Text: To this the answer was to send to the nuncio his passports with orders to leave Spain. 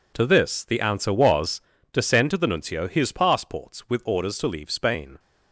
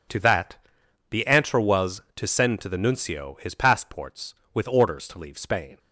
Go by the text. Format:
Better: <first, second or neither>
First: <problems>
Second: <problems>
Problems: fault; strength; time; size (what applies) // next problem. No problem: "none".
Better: first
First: none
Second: says "that" for "this"; at 0.1 s